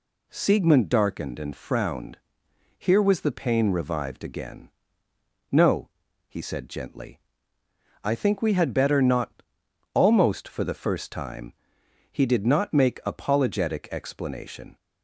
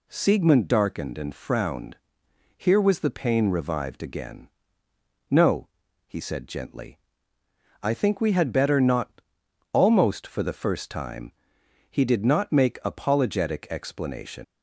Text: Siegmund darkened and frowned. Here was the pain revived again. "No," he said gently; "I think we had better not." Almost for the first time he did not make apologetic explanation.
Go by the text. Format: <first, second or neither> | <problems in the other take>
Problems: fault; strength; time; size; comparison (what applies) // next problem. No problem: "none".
first | pauses between "time" and "he"; noticeable; at 11.3 s; 0.58 s long; noticeable in the first // leaves "explanation" unfinished; at 14.4 s; 105 ms